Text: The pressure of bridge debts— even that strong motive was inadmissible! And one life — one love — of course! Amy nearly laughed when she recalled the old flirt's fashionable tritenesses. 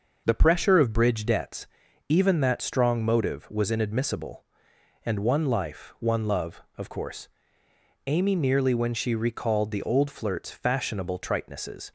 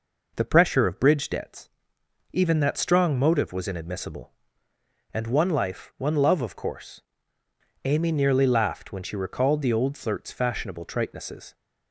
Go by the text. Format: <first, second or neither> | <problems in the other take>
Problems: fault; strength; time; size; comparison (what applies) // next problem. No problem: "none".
second | skips "laughed"; at 8.7 s